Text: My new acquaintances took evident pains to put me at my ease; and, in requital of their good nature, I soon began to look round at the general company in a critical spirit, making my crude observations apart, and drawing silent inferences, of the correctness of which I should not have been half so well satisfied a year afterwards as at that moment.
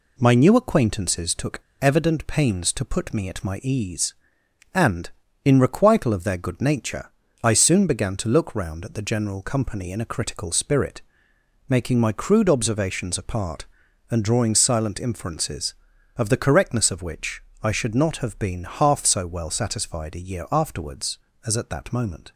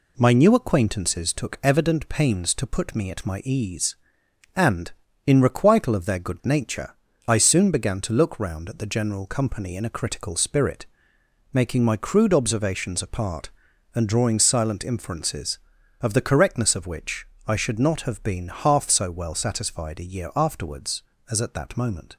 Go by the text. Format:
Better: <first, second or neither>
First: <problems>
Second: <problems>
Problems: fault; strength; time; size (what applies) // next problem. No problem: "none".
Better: second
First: pauses between "took" and "evident"; slight; at 1.5 s; 0.20 s long // pauses between "which" and "I"; slight; at 17.4 s; 0.22 s long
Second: pauses between "which" and "I"; slight; at 17.2 s; 0.22 s long